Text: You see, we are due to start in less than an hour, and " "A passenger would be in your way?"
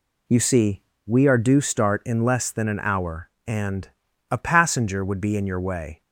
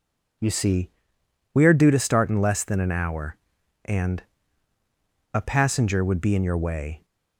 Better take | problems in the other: second | skips "to"; at 1.6 s

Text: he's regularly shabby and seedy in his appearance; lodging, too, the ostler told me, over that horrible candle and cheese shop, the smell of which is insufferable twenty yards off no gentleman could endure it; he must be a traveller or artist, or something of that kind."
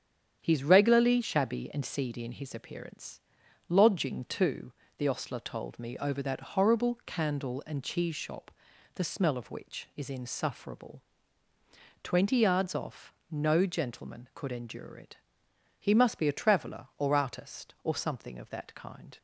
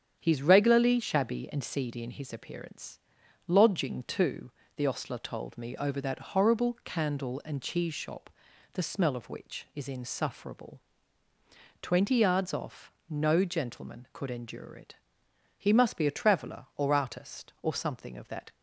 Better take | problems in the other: first | starts louder than the rest; strong; until 1.2 s; 8.5 dB; strong in the first // pauses between "insufferable" and "twenty"; at 10.7 s; 1.0 s long; also in the first // pauses between "off" and "no"; slight; at 12.9 s; 0.16 s long; slight in the first // stops before "kind"; at 18.5 s

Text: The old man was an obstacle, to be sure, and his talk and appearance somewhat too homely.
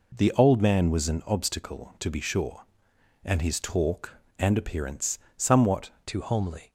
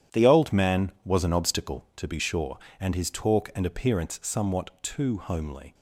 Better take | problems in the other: second | pauses between "appearance" and "somewhat"; slight; at 5.1 s; 0.20 s long // changes voice at "too"; from 6.0 s on; 0.7 s long

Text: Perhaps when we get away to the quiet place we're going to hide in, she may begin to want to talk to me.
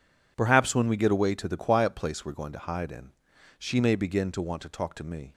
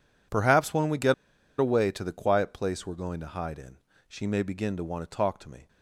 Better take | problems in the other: first | pauses between "get" and "away"; at 1.1 s; 0.45 s long

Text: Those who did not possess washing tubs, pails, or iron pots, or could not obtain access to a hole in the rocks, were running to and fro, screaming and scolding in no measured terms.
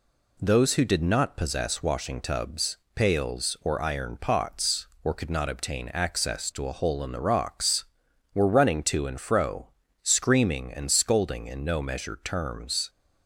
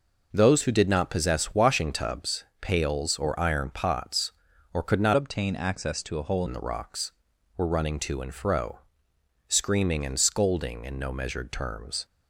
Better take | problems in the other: first | changes voice from "obtain" to "hole"; from 5.1 to 6.4 s; 1.3 s long

